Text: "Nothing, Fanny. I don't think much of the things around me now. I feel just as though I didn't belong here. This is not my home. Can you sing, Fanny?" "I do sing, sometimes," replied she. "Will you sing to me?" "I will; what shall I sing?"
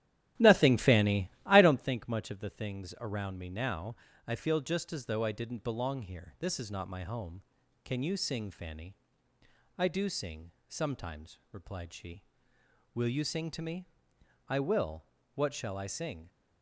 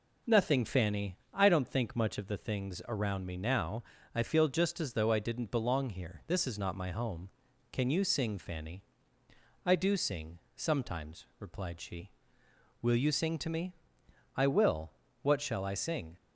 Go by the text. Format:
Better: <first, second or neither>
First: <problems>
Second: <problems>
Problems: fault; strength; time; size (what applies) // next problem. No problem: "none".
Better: second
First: starts louder than the rest; strong; until 2.0 s; 12 dB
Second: none